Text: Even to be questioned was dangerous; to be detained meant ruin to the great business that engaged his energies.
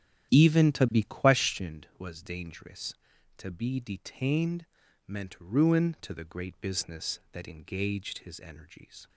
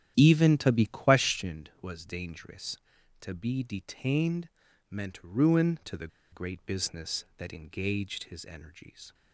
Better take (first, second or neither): first